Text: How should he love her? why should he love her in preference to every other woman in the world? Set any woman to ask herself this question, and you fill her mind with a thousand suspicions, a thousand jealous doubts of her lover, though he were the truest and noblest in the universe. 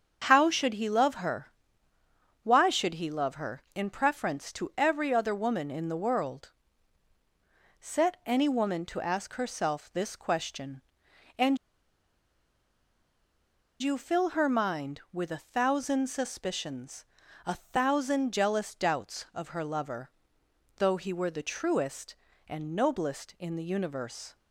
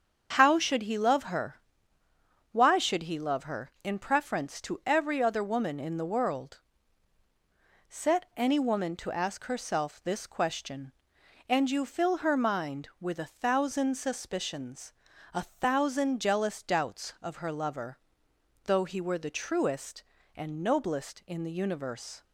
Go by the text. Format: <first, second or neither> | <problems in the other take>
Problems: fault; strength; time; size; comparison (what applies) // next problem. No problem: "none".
second | starts louder than the rest; strong; until 1.2 s; 7 dB; strong in the second // pauses between "and" and "you"; strong; at 11.5 s; 2.2 s long